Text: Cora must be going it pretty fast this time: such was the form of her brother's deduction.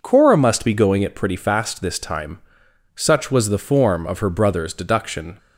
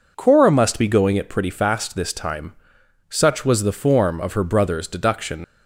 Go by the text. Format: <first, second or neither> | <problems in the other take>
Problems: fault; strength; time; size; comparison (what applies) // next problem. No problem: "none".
first | leaves "deduction" unfinished; at 5.4 s; 70 ms